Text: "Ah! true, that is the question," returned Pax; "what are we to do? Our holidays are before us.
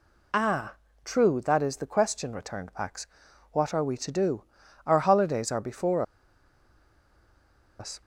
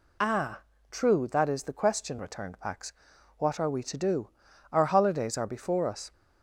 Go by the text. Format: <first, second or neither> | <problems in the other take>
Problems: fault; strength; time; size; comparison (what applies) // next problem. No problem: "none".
second | pauses between "before" and "us"; strong; at 6.0 s; 1.7 s long